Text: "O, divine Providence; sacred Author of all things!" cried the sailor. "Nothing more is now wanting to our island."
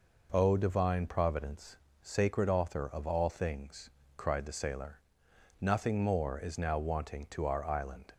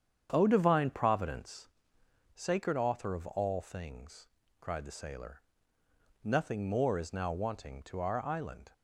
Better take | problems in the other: first | starts louder than the rest; strong; until 1.6 s; 8.5 dB

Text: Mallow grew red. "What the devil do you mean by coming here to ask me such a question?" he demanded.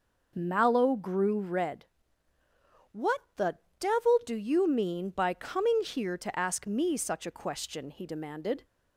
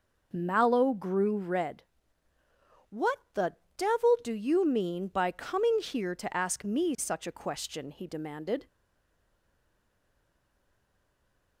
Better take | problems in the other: first | pauses between "What" and "the"; slight; at 3.1 s; 0.16 s long; slight in the first // pauses between "the" and "devil"; slight; at 3.5 s; 0.20 s long; slight in the first // stays silent after the last word; strong; from 8.6 s on; 2.9 s long

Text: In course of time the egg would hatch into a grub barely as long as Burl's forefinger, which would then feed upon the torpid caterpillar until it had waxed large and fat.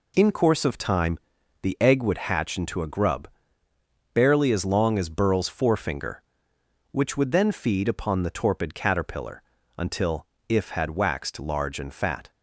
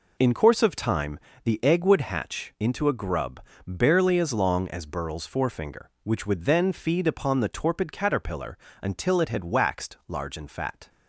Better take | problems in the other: second | pauses between "time" and "the"; at 1.1 s; 0.42 s long; slight in the second // pauses between "grub" and "barely"; noticeable; at 3.2 s; 0.86 s long; slight in the second // pauses between "caterpillar" and "until"; slight; at 9.4 s; 0.36 s long; slight in the second // says "if" for "it"; at 10.4 s

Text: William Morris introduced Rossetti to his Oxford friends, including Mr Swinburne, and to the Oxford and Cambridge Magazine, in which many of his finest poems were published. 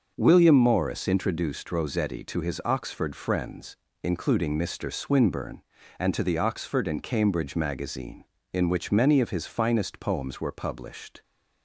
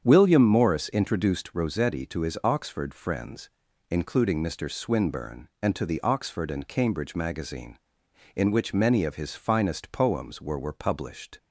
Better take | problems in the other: first | starts louder than the rest; strong; until 1.0 s; 8 dB; noticeable in the first // says "were" twice; at 10.5 s

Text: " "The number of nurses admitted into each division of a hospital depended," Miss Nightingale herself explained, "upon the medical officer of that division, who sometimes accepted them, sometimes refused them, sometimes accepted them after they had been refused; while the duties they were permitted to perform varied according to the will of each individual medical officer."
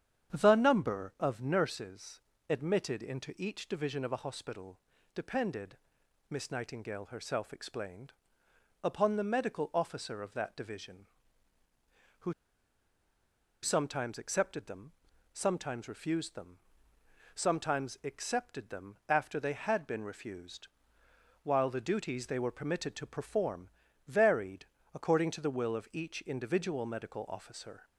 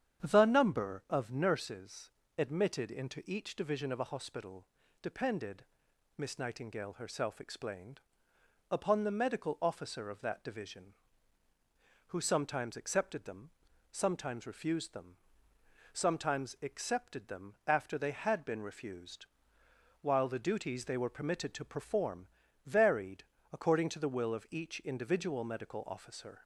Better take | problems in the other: second | starts louder than the rest; strong; until 1.3 s; 9 dB; strong in the second // pauses between "nurses" and "admitted"; slight; at 2.2 s; 0.28 s long; slight in the second // pauses between "hospital" and "depended"; slight; at 4.7 s; 0.34 s long; slight in the second // pauses between "who" and "sometimes"; strong; at 12.3 s; 1.3 s long // pauses between "perform" and "varied"; at 23.6 s; 0.40 s long; also in the second // pauses between "varied" and "according"; slight; at 24.6 s; 0.30 s long; slight in the second

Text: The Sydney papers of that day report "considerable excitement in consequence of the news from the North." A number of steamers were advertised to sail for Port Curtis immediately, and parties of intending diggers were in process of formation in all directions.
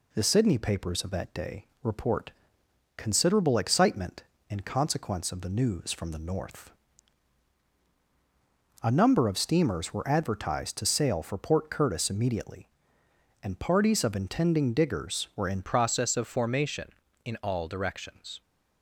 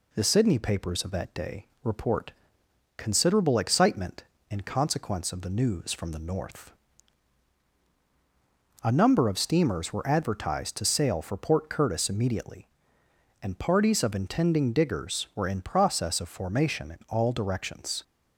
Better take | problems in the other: second | pauses between "day" and "report"; slight; at 1.6 s; 0.18 s long; slight in the second // pauses between "report" and "considerable"; noticeable; at 2.3 s; 0.64 s long; noticeable in the second // changes voice at "process"; from 15.6 s on; 2.8 s long

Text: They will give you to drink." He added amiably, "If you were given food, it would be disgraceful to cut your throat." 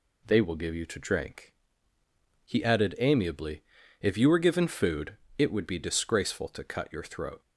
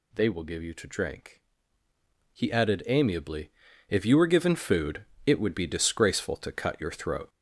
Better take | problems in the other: first | gets louder; noticeable; throughout; 5.5 dB

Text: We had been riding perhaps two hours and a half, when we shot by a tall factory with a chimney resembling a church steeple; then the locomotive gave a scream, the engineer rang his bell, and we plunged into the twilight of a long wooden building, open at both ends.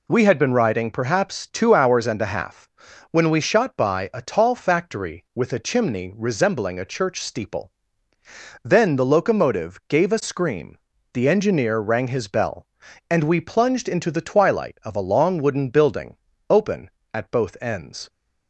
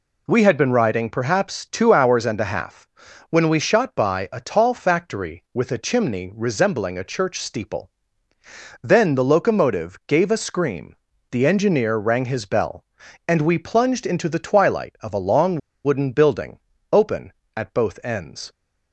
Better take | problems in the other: first | pauses between "long" and "wooden"; slight; at 15.5 s; 0.25 s long

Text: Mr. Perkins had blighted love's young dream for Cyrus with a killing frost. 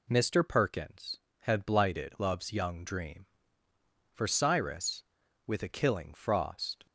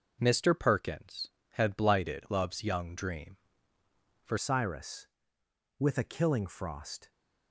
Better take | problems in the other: first | changes voice at "Cyrus"; from 4.3 s on; 2.8 s long

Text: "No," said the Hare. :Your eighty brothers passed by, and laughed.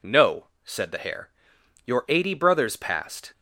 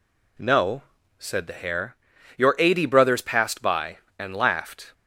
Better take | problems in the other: second | stops before "by and laughed"; at 3.3 s

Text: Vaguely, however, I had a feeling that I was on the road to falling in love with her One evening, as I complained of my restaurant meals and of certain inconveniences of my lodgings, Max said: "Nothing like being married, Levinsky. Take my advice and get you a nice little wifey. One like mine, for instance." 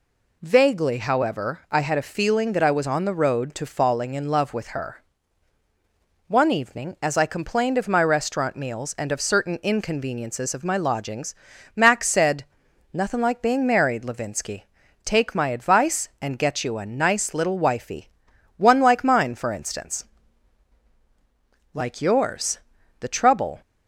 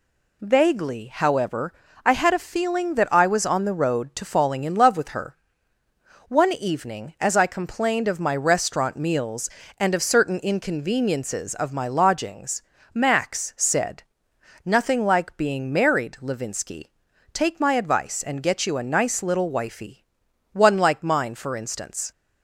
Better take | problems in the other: second | pauses between "her" and "One"; strong; at 5.0 s; 1.2 s long; noticeable in the second // goes on to say "Like yours The trouble"; strong; from 21.7 s on; 1.8 s long

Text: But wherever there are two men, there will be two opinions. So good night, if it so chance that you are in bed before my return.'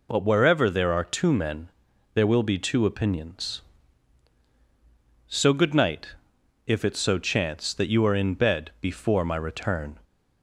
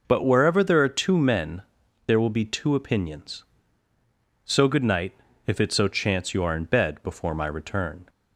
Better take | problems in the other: first | skips "that"; at 6.3 s

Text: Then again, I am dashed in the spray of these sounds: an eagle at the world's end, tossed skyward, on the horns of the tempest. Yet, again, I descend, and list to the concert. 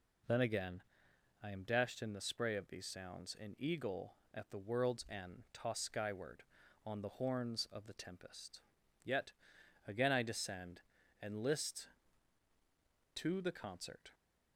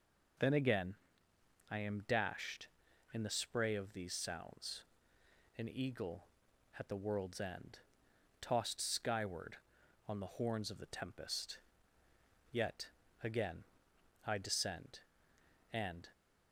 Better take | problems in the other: first | stops before "list to the concert"; at 16.1 s

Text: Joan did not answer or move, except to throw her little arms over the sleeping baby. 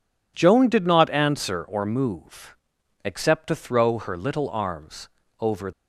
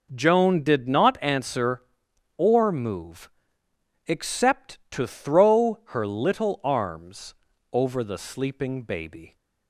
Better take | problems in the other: second | pauses between "arms" and "over"; slight; at 5.0 s; 0.32 s long; slight in the second // stops before "the sleeping baby"; at 5.7 s

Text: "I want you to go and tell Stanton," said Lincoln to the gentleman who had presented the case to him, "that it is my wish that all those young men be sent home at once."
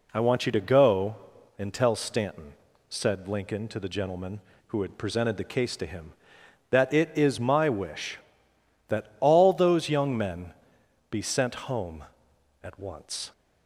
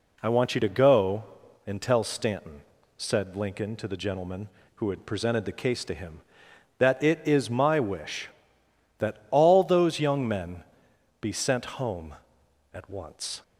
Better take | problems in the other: neither | pauses between "men" and "be"; noticeable; the same in both

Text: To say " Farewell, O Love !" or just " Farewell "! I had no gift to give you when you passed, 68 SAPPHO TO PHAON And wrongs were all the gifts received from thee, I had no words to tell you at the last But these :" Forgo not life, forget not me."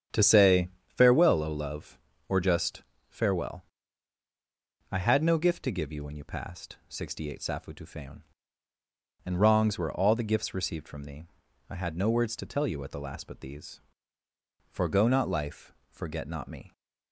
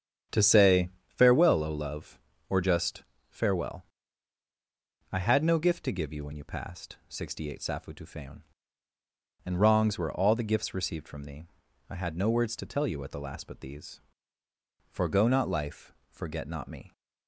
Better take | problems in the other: neither | starts louder than the rest; strong; the same in both

